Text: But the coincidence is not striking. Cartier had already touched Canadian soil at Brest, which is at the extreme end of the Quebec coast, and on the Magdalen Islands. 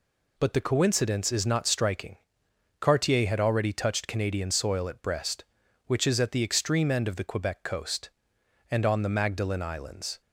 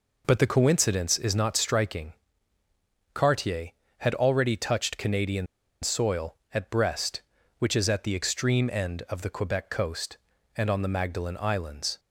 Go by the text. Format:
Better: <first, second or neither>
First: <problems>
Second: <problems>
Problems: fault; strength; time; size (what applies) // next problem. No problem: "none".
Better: first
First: none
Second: pauses between "Canadian" and "soil"; slight; at 5.4 s; 0.36 s long